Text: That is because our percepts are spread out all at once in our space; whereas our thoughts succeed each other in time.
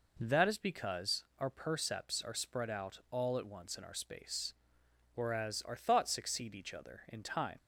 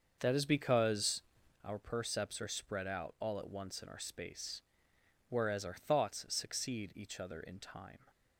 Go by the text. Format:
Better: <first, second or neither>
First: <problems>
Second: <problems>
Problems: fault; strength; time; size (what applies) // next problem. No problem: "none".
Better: first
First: none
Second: starts louder than the rest; until 1.6 s; 6.5 dB // pauses between "because" and "our"; at 1.2 s; 0.42 s long